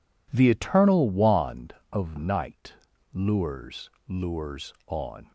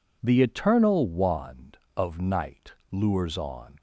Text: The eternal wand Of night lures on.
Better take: second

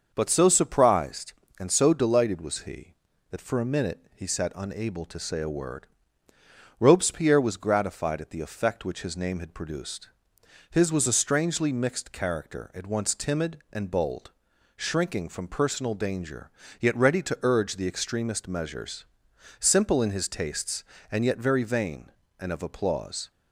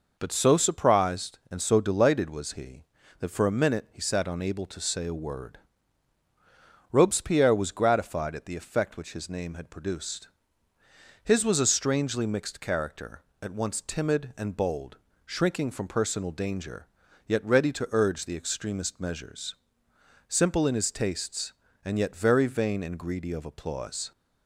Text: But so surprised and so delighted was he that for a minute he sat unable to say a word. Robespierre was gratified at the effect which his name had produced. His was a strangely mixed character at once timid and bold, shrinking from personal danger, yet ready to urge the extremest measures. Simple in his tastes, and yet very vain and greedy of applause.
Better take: second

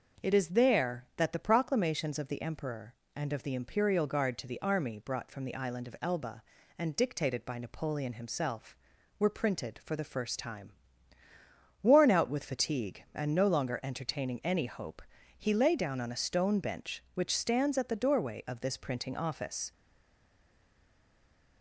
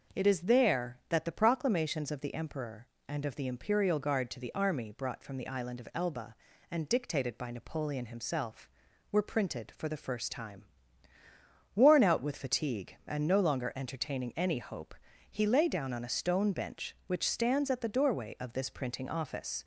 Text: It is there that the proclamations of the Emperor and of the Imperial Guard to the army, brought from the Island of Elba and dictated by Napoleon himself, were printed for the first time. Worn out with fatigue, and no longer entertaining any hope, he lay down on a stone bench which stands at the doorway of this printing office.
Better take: second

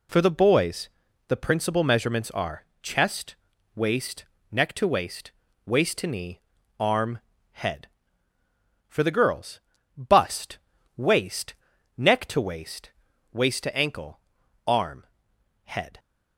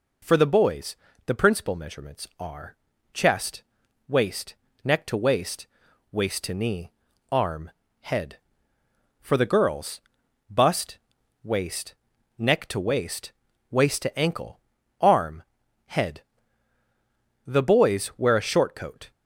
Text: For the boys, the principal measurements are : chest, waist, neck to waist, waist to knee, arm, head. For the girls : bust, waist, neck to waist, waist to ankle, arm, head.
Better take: first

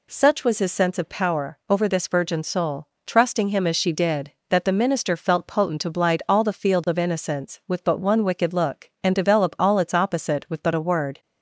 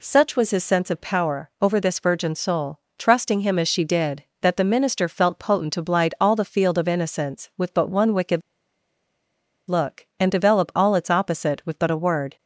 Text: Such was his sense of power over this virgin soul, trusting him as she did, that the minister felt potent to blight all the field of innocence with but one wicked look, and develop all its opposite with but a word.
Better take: first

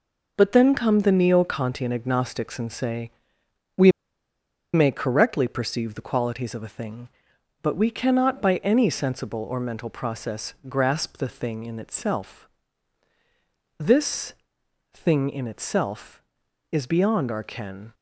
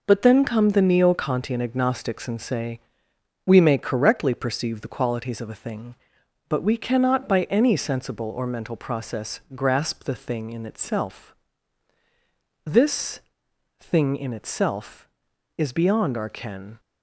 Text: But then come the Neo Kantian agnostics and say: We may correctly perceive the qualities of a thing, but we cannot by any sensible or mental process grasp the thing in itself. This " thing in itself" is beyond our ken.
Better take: second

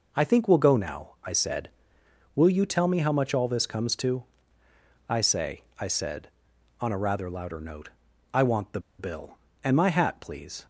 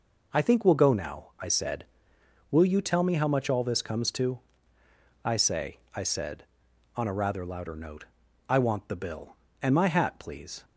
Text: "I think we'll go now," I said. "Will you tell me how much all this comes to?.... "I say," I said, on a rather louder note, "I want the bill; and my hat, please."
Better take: second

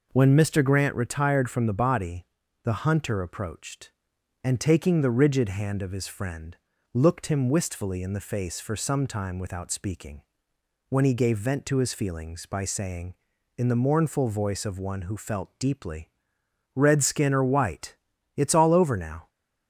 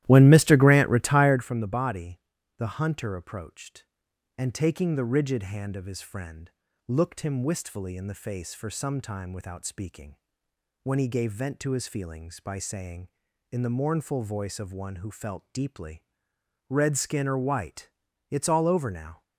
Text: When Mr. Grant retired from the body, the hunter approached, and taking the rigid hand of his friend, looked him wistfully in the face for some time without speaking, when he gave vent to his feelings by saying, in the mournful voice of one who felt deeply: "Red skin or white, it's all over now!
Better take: first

